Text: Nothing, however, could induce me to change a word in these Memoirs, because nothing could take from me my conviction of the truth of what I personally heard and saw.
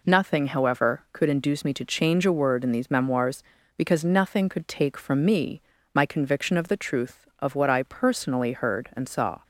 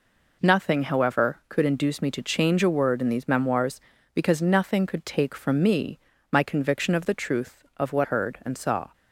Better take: first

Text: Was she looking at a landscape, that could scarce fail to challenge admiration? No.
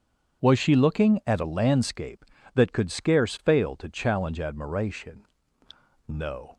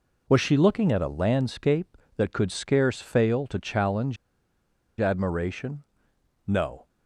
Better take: first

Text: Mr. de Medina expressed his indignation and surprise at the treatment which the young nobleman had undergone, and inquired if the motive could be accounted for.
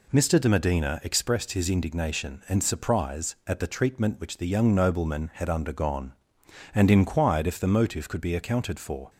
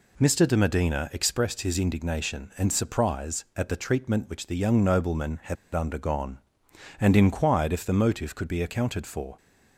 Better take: first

